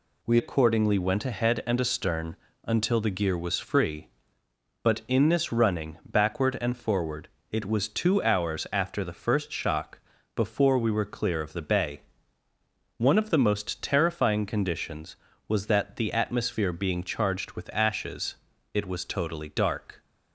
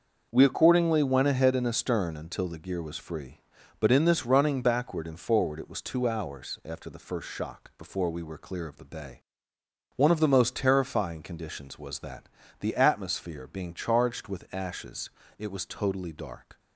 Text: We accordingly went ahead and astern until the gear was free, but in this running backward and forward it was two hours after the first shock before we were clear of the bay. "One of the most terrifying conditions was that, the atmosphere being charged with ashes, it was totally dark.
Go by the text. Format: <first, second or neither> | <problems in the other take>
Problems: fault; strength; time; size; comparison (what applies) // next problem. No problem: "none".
second | changes voice at "accordingly"; from 0.3 s on; 19.6 s long // pauses between "astern" and "until"; slight; at 2.3 s; 0.28 s long // pauses between "forward" and "it"; slight; at 7.2 s; 0.22 s long // pauses between "shock" and "before"; at 9.9 s; 0.38 s long